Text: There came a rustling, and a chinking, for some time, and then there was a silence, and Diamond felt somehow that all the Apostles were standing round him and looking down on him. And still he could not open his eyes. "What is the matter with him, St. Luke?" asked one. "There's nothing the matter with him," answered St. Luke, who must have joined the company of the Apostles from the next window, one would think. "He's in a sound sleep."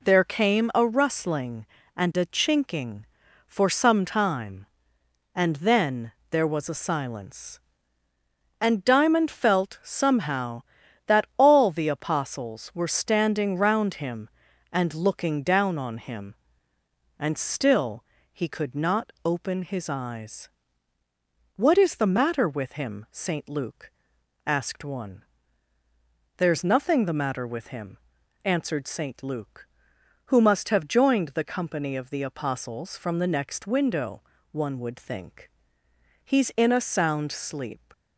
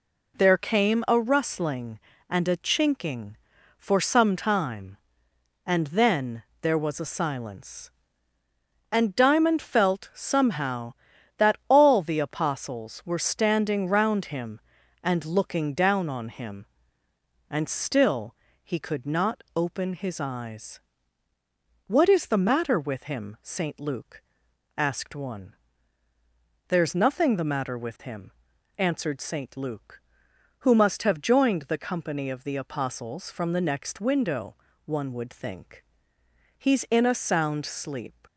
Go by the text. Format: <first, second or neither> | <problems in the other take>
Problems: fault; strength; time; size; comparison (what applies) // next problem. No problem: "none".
neither | pauses between "then" and "there"; slight; the same in both // pauses between "still" and "he"; slight; the same in both